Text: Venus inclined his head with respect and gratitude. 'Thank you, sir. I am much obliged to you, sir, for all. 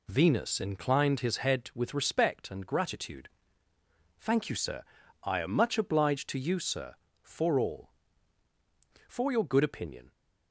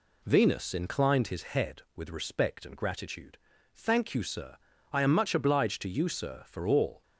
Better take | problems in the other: second | goes on to say "For your good opinion"; noticeable; from 9.0 s on; 1.0 s long

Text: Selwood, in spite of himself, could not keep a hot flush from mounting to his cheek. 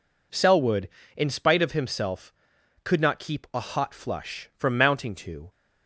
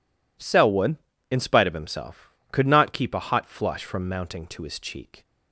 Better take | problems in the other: second | stops before "his cheek"; at 5.4 s

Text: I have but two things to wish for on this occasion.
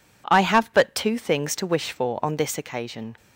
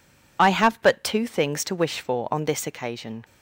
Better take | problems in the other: first | loses the start of "I"; at 0.3 s; 65 ms

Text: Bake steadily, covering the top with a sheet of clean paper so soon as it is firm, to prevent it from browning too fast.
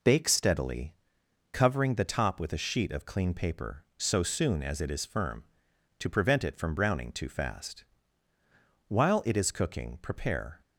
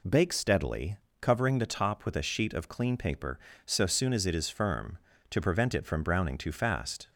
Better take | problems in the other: second | goes on to say "While it is cooking prepare"; strong; from 8.8 s on; 1.7 s long

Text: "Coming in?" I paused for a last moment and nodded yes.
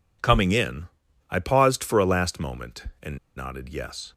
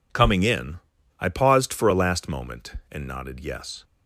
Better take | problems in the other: second | pauses between "and" and "nodded"; slight; at 3.1 s; 0.19 s long

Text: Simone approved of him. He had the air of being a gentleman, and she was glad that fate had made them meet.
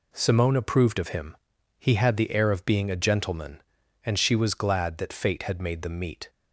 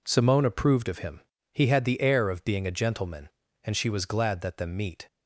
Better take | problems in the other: first | skips "fate had made"; at 4.5 s

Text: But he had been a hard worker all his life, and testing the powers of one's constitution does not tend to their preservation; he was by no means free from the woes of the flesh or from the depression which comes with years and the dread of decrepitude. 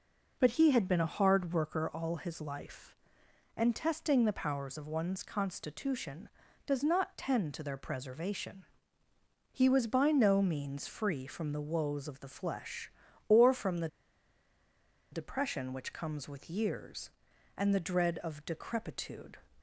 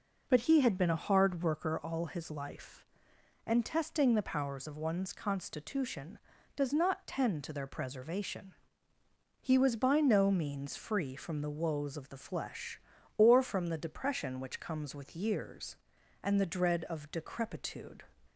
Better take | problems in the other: second | pauses between "the" and "depression"; strong; at 13.8 s; 1.2 s long

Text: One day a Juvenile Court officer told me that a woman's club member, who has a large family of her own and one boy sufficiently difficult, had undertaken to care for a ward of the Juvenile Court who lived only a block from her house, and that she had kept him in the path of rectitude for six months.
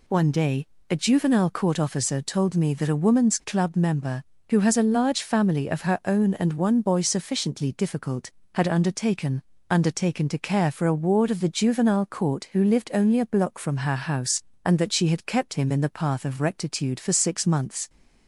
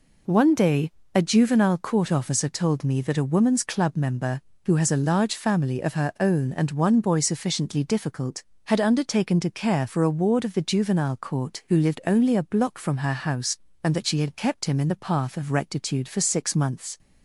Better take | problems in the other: second | pauses between "day" and "a"; slight; at 0.6 s; 0.24 s long; slight in the second // says "undertaken" twice; at 9.6 s

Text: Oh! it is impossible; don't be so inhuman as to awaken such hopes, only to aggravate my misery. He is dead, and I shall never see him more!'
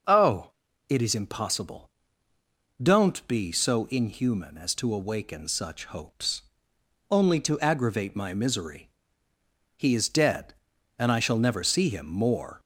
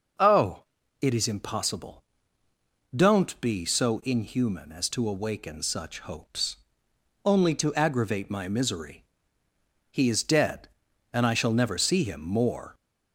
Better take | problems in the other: neither | none

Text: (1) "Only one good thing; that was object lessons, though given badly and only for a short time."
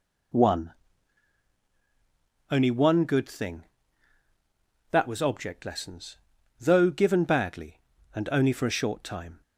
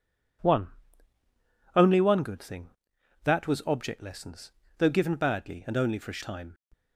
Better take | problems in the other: first | skips "short"; at 6.2 s

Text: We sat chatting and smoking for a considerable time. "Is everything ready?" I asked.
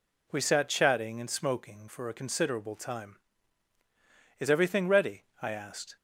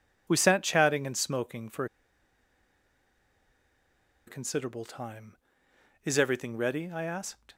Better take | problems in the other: first | pauses between "for" and "a"; strong; at 1.8 s; 2.4 s long

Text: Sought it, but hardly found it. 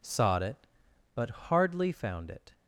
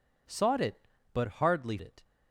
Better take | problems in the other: first | skips "found"; at 1.7 s

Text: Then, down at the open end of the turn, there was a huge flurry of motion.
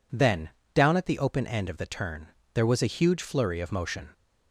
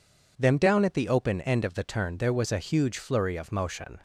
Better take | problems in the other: first | says "Them" for "Then"; at 0.3 s

